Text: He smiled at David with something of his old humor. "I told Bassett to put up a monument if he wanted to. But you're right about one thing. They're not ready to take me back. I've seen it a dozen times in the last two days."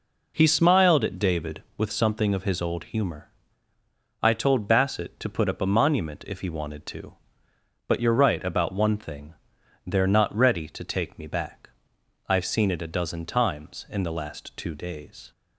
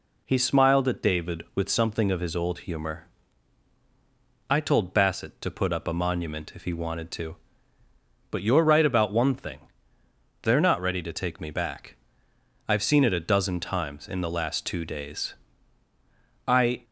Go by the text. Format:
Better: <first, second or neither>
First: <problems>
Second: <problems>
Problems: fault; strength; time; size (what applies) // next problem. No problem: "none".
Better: first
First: none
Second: goes on to say "I"; slight; from 16.4 s on; 0.36 s long